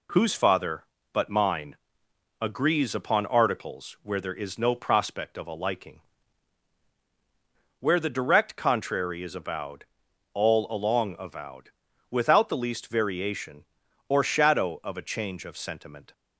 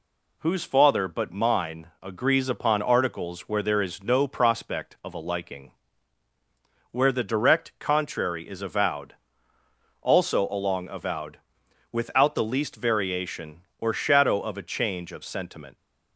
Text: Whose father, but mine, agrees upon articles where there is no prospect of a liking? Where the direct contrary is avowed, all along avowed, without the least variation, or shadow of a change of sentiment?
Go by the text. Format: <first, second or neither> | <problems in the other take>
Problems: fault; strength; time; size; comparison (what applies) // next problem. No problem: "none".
first | says "also" for "all"; at 10.0 s